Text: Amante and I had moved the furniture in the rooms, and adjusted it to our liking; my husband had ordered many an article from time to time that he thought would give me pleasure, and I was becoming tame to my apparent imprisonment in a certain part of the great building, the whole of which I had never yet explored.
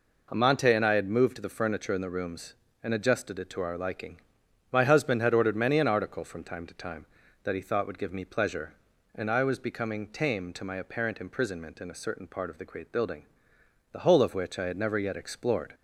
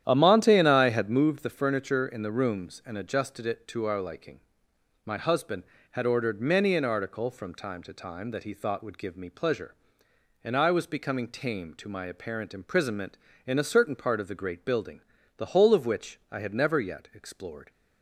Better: first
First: none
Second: starts louder than the rest; strong; until 1.3 s; 10.5 dB

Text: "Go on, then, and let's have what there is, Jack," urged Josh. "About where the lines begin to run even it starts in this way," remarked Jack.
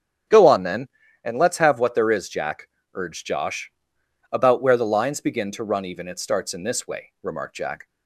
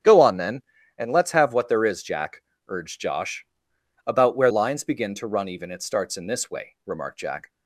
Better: first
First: starts louder than the rest; strong; until 1.6 s; 9 dB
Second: starts louder than the rest; strong; until 1.4 s; 9 dB // skips "the"; at 4.4 s

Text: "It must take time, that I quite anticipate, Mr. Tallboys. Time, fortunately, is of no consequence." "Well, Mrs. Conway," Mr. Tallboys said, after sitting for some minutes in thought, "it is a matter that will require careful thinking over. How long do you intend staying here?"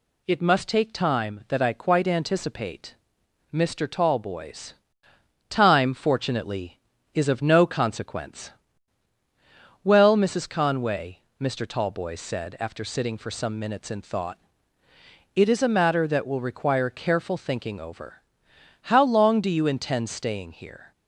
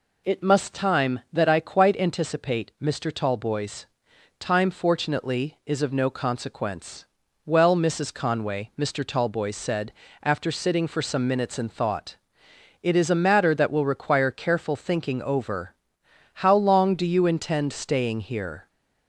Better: first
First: none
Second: skips "take"; at 0.7 s

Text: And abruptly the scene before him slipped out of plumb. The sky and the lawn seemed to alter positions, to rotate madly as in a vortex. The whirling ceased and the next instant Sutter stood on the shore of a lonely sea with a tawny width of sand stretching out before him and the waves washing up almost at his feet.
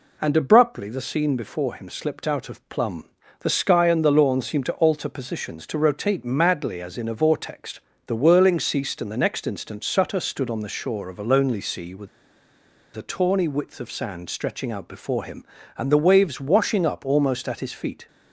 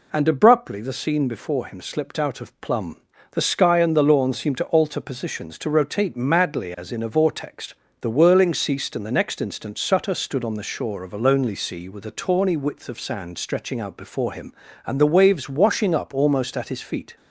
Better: second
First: pauses between "with" and "a"; noticeable; at 12.0 s; 0.88 s long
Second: none

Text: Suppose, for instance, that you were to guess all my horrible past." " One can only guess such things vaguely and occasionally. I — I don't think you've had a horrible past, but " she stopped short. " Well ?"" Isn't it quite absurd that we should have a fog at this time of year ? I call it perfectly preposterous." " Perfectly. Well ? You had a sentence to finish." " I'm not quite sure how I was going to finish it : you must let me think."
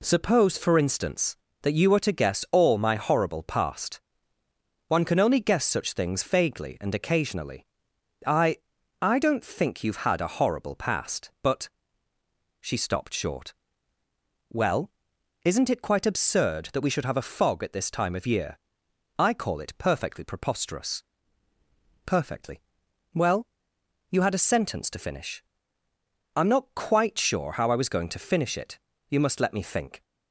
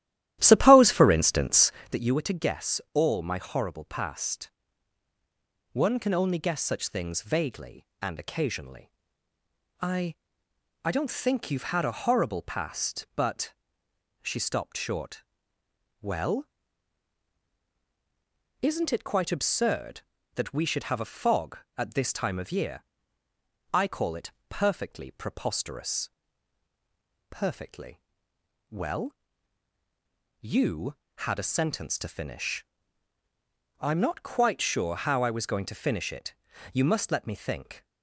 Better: first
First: none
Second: starts louder than the rest; strong; until 2.0 s; 14 dB // pauses between "it" and "perfectly"; slight; at 24.3 s; 0.18 s long

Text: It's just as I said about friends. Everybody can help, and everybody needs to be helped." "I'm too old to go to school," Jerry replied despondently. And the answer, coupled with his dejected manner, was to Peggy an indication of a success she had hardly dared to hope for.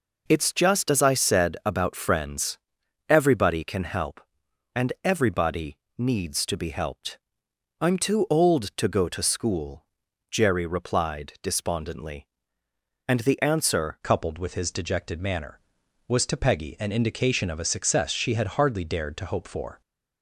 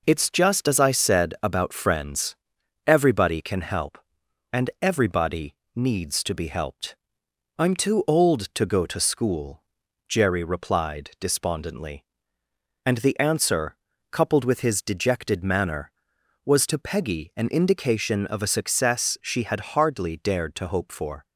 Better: second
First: pauses between "everybody" and "needs"; slight; at 5.7 s; 0.20 s long // changes voice at "coupled"; from 14.0 s on; 5.8 s long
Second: pauses between "everybody" and "needs"; slight; at 5.5 s; 0.20 s long

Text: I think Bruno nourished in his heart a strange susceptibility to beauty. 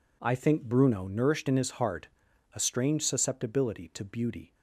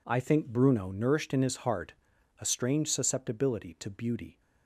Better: neither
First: pauses between "heart" and "a"; noticeable; at 2.0 s; 0.48 s long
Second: pauses between "heart" and "a"; noticeable; at 1.9 s; 0.48 s long

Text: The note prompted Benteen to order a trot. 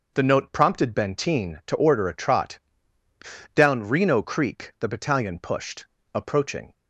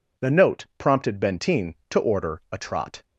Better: second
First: starts louder than the rest; until 1.1 s; 6 dB // goes on to say "Down Reno Creek the battalion pushed approaching"; strong; from 3.5 s on; 3.1 s long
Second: none

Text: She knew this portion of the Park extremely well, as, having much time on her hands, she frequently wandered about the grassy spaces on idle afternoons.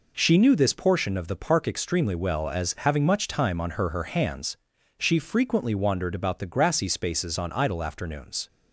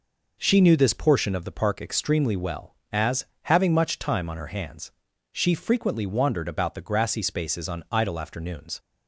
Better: second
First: says "her" twice; at 3.8 s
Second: none

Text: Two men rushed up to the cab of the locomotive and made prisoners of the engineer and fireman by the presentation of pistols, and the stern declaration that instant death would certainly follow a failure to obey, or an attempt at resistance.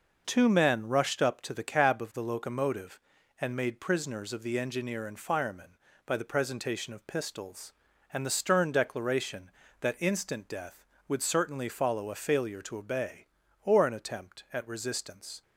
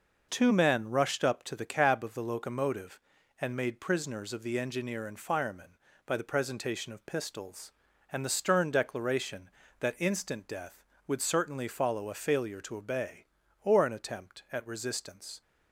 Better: neither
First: none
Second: none

